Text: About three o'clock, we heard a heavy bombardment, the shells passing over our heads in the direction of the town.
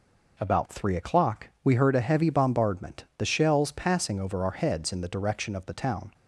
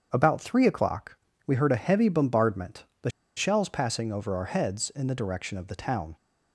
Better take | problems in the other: first | starts louder than the rest; strong; until 1.1 s; 7.5 dB // pauses between "the" and "shells"; slight; at 3.1 s; 0.26 s long

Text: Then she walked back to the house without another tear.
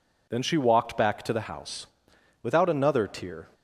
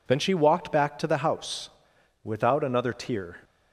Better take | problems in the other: neither | pauses between "house" and "without"; noticeable; the same in both

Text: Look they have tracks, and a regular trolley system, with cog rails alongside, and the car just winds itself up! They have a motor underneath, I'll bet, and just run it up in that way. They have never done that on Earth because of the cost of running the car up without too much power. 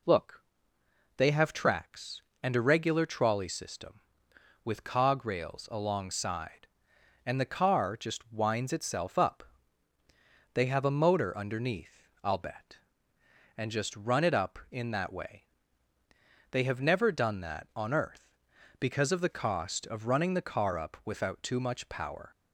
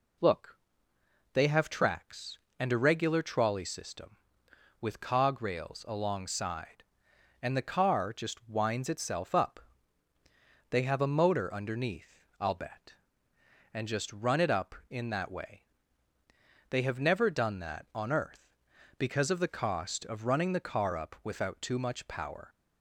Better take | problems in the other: neither | pauses between "Look" and "they"; noticeable; the same in both

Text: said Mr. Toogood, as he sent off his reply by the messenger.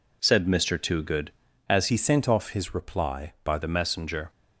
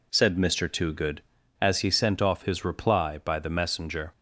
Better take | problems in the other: second | changes voice from "he" to "by"; from 1.8 to 3.5 s; 1.7 s long

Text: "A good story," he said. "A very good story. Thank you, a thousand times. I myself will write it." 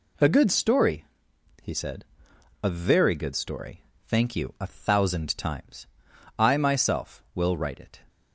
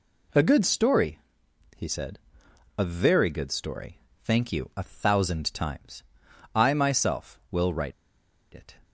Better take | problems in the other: first | pauses between "write" and "it"; noticeable; at 7.9 s; 0.61 s long

